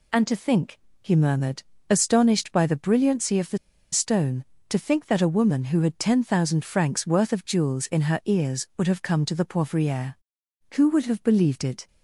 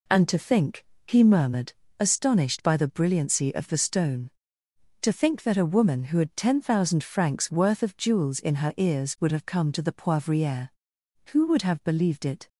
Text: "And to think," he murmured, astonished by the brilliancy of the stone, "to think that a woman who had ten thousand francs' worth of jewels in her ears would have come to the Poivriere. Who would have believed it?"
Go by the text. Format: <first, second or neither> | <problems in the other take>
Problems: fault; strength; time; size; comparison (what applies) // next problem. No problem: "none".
second | pauses between "the" and "stone"; slight; at 3.5 s; 0.35 s long